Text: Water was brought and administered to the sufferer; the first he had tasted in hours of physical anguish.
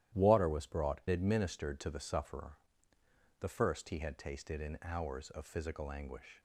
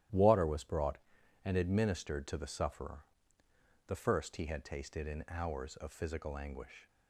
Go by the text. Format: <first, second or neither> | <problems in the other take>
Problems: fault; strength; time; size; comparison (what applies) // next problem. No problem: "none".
second | starts louder than the rest; strong; until 1.2 s; 13 dB; strong in the second // skips "and"; at 1.0 s